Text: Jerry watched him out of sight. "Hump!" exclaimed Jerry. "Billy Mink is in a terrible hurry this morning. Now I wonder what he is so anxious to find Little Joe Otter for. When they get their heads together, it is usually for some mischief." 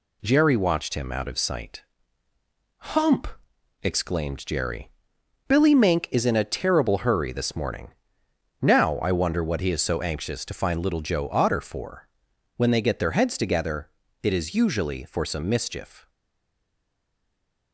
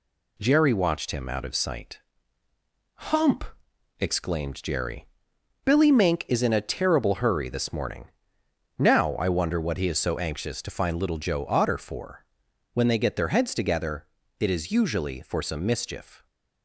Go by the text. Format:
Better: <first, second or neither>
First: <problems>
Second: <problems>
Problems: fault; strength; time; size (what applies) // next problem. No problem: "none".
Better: second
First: stays silent after the last word; noticeable; from 16.0 s on; 1.7 s long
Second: none